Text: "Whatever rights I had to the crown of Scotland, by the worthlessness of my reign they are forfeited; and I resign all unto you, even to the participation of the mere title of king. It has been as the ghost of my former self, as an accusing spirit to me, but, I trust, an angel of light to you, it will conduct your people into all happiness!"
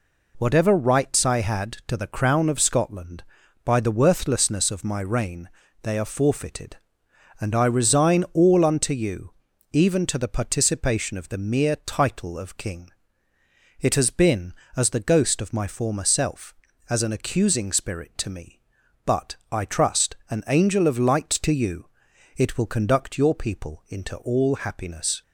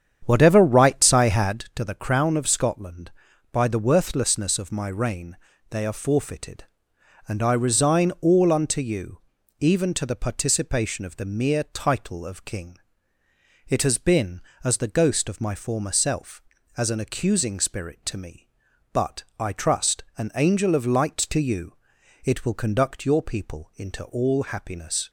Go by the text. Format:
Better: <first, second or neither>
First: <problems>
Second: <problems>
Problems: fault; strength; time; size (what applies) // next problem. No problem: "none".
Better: first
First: pauses between "reign" and "they"; slight; at 5.4 s; 0.34 s long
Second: starts louder than the rest; strong; until 1.7 s; 8.5 dB // pauses between "reign" and "they"; slight; at 5.3 s; 0.34 s long